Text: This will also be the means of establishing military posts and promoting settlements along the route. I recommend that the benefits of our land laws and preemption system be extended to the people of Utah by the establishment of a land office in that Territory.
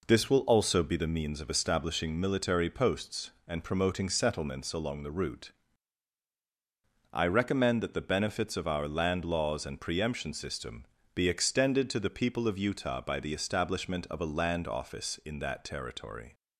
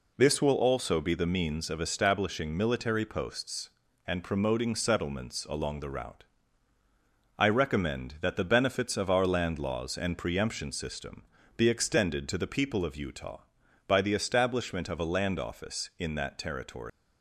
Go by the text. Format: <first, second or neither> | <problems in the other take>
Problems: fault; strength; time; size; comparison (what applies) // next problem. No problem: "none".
first | pauses between "system" and "be"; slight; at 11.2 s; 0.32 s long; slight in the first // leaves "Territory" unfinished; at 16.8 s; 140 ms